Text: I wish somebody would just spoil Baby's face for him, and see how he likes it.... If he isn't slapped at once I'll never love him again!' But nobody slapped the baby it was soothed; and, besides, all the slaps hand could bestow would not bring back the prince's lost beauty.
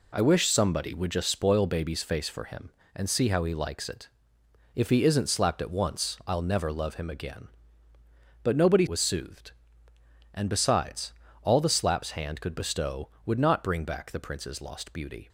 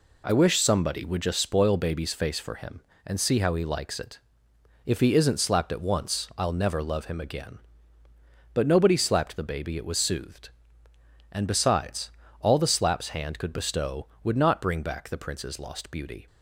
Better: second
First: skips "slapped the baby it"; at 8.8 s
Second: none

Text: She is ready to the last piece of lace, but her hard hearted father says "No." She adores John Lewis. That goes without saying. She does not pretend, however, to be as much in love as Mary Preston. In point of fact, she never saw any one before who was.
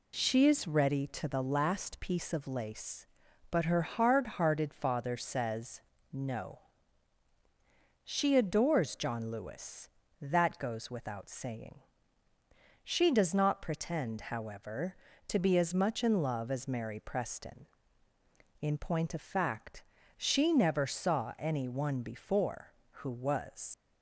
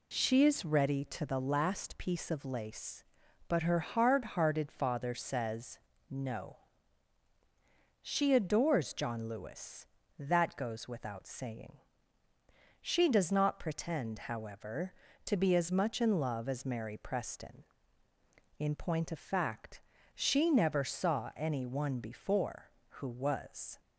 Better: second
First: pauses between "says" and "No"; slight; at 5.8 s; 0.32 s long // leaves "was" unfinished; at 23.7 s; 85 ms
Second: pauses between "says" and "No"; slight; at 5.7 s; 0.32 s long

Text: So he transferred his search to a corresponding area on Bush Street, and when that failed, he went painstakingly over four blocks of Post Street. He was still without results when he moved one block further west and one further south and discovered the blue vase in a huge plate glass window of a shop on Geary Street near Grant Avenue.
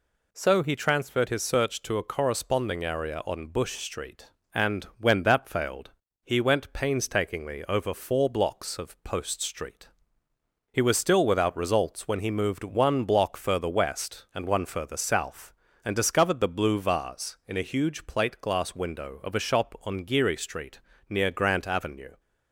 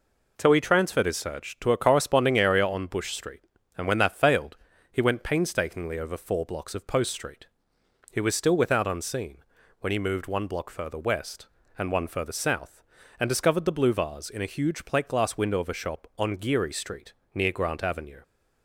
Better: first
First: pauses between "Street" and "near"; slight; at 20.7 s; 0.30 s long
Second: says "unseen" for "results"; at 8.8 s // pauses between "Street" and "near"; slight; at 17.1 s; 0.20 s long

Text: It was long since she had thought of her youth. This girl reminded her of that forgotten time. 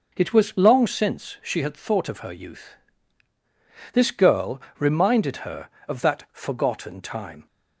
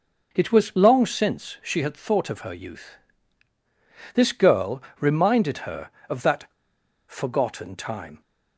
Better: first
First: pauses between "girl" and "reminded"; slight; at 4.5 s; 0.18 s long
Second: pauses between "girl" and "reminded"; slight; at 4.8 s; 0.18 s long // pauses between "that" and "forgotten"; noticeable; at 6.4 s; 0.62 s long

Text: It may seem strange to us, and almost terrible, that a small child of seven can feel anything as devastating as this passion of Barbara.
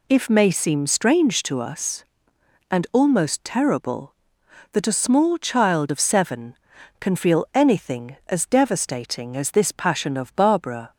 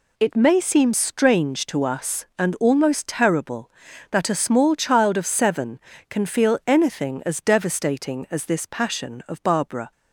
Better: second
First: says "If" for "It"; at 0.0 s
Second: none

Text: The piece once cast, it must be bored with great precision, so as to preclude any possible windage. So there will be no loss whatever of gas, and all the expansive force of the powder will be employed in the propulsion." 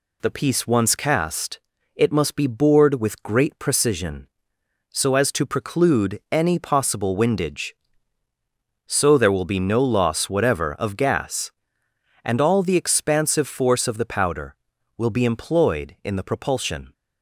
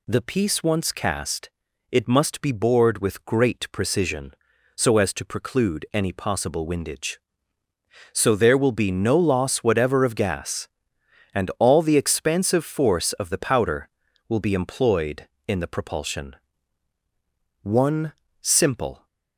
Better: first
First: none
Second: goes on to say "One simple"; from 17.6 s on; 1.4 s long

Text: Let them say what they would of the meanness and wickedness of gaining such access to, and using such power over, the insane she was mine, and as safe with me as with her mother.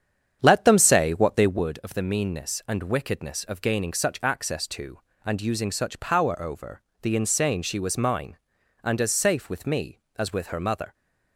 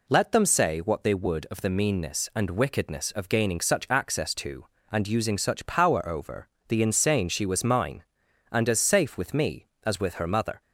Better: second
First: starts louder than the rest; strong; until 1.7 s; 8.5 dB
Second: none

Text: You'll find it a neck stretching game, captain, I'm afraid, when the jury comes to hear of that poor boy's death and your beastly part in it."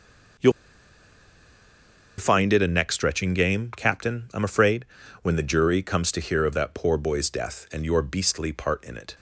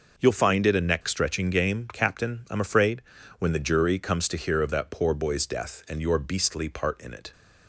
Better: second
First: pauses between "You'll" and "find"; strong; at 0.5 s; 1.6 s long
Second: none

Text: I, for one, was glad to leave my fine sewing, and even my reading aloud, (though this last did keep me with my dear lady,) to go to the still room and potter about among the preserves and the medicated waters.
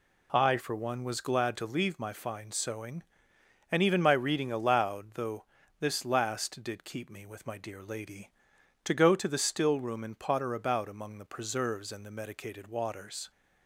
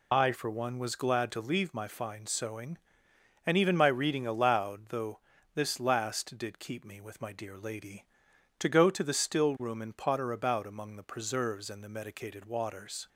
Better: first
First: pauses between "though" and "this"; at 5.4 s; 0.38 s long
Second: loses the start of "I"; at 0.1 s; 70 ms // pauses between "though" and "this"; at 5.1 s; 0.38 s long

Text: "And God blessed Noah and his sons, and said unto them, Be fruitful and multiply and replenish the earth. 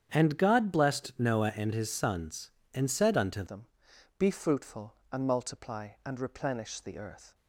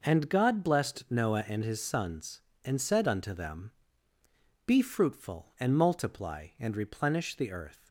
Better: second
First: starts louder than the rest; strong; until 1.1 s; 8.5 dB // changes voice at "them"; from 3.4 s on; 3.9 s long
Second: none

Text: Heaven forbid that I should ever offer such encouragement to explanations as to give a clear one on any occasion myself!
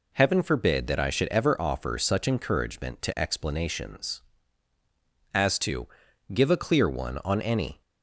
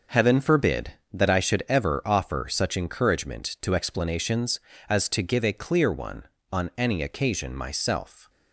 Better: second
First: pauses between "to" and "give"; noticeable; at 5.8 s; 0.46 s long // stops before "occasion myself"; at 7.8 s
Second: none

